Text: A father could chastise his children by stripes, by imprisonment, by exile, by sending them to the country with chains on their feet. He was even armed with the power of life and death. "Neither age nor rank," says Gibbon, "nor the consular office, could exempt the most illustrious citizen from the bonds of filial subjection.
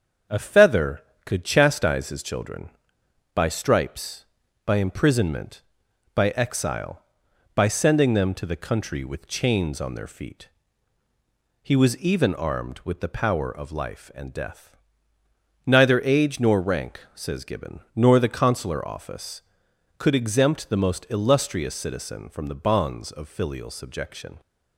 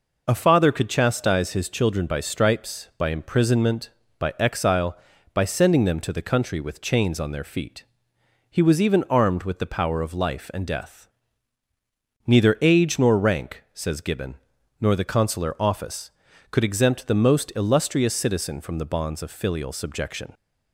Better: second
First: starts louder than the rest; strong; until 1.5 s; 7 dB // says "feather" for "father"; at 0.3 s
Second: none

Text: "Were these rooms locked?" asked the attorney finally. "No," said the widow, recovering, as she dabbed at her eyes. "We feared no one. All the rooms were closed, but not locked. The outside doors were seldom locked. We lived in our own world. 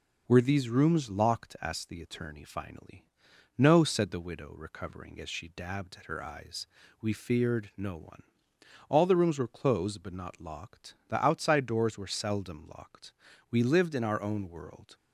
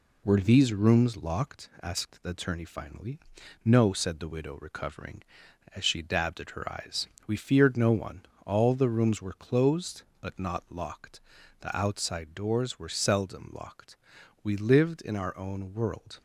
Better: neither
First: none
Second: none

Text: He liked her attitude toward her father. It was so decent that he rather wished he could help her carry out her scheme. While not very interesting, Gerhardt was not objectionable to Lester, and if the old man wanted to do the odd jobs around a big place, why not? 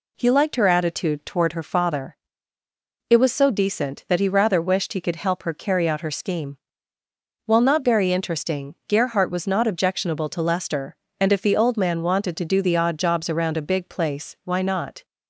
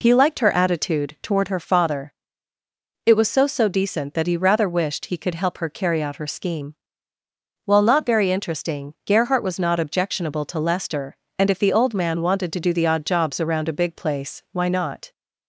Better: first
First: none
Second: says "so" twice; at 3.4 s

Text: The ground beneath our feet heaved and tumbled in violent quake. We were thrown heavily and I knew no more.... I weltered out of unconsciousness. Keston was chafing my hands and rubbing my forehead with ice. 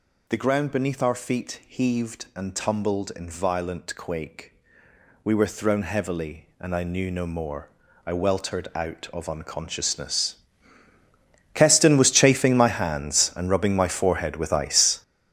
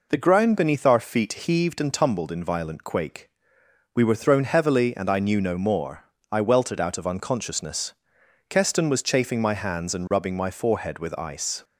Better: second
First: gets louder; strong; throughout; 10 dB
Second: none

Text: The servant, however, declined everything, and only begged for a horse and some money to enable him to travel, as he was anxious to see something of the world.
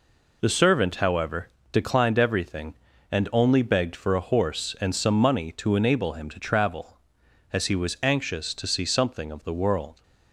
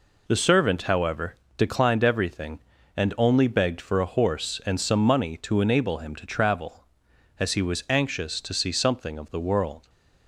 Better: neither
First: none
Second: none

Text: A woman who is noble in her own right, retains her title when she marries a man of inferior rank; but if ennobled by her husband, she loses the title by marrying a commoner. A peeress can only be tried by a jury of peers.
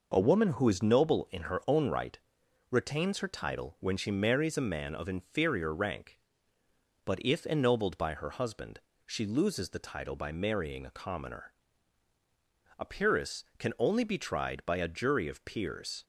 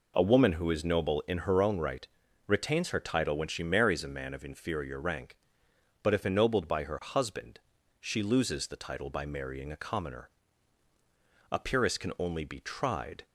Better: first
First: none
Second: stops before "by a jury of peers"; at 13.2 s

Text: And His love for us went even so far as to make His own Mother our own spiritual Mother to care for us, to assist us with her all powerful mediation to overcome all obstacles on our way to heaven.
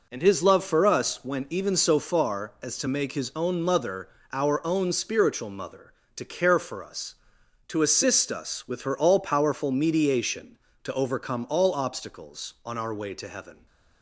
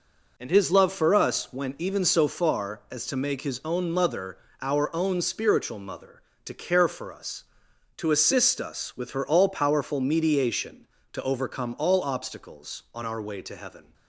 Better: neither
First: pauses between "Mother" and "our"; slight; at 4.0 s; 0.24 s long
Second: pauses between "Mother" and "our"; slight; at 4.3 s; 0.24 s long

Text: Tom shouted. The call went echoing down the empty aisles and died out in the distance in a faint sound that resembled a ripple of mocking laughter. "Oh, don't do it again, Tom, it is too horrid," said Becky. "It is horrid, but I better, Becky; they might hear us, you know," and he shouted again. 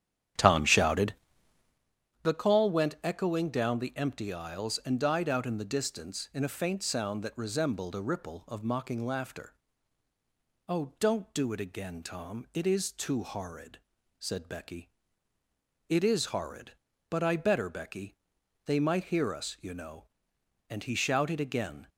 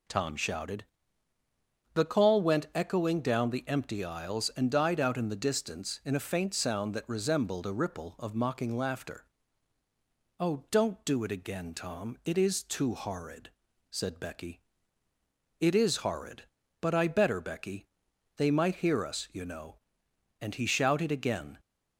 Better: second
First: starts louder than the rest; strong; until 1.9 s; 10 dB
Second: none

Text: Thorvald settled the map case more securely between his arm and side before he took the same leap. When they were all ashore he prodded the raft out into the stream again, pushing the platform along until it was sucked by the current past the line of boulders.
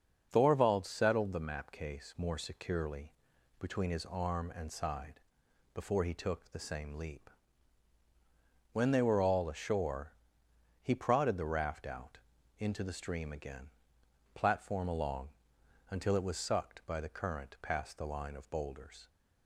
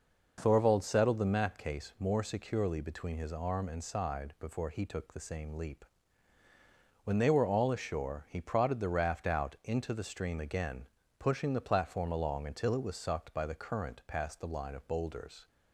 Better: second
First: starts louder than the rest; until 1.3 s; 6.5 dB // pauses between "securely" and "between"; noticeable; at 3.1 s; 0.48 s long // pauses between "side" and "before"; noticeable; at 5.1 s; 0.52 s long // pauses between "ashore" and "he"; noticeable; at 10.1 s; 0.70 s long // pauses between "out" and "into"; at 12.1 s; 0.40 s long // skips "pushing the"; at 14.0 s // pauses between "along" and "until"; noticeable; at 15.2 s; 0.60 s long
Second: none

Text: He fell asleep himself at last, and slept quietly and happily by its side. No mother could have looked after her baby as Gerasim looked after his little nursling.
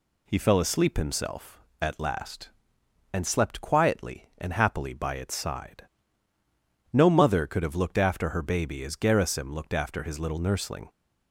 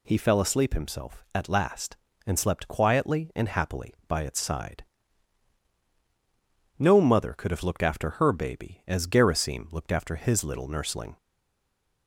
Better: first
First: none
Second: stays silent after the last word; slight; from 11.1 s on; 0.9 s long

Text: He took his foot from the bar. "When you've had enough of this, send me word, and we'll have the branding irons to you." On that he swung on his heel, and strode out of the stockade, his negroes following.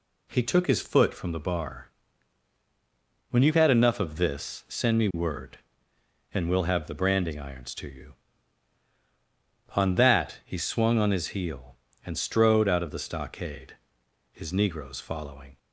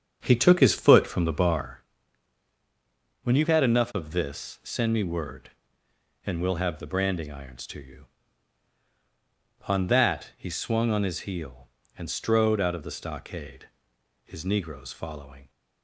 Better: first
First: none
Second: starts louder than the rest; strong; until 1.7 s; 7 dB

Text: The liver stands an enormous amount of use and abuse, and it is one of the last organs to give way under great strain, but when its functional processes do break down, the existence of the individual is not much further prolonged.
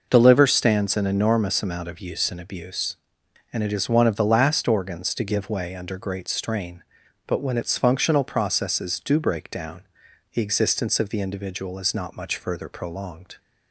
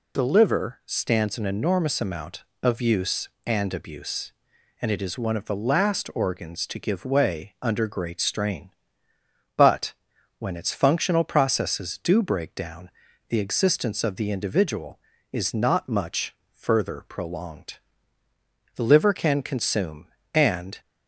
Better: first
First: none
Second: pauses between "but" and "when"; noticeable; at 9.9 s; 0.46 s long // pauses between "much" and "further"; slight; at 16.3 s; 0.16 s long // goes on to say "The liver can consume and"; strong; from 18.7 s on; 2.0 s long

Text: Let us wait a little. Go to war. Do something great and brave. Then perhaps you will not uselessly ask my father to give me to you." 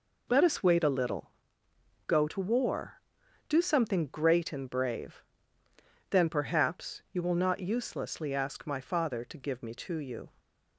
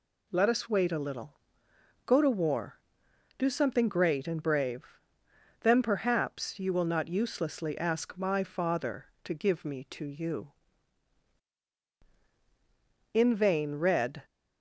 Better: first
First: none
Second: goes on to say "In vain Red"; noticeable; from 13.1 s on; 1.1 s long

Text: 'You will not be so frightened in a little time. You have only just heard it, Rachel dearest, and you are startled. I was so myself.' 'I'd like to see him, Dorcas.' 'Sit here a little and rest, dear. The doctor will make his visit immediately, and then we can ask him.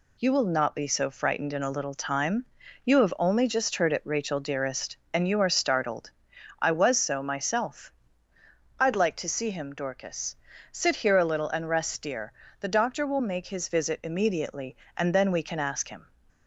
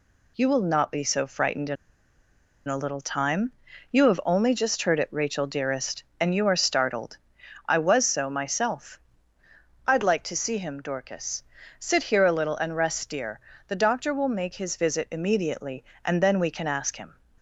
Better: first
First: none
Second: pauses between "in" and "a"; noticeable; at 1.7 s; 0.92 s long

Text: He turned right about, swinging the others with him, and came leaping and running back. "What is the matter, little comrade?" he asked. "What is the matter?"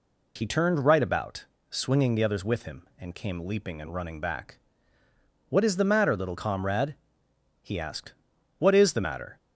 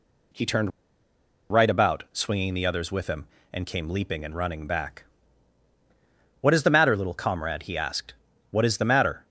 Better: first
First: none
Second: pauses between "turned" and "right"; noticeable; at 0.7 s; 0.81 s long

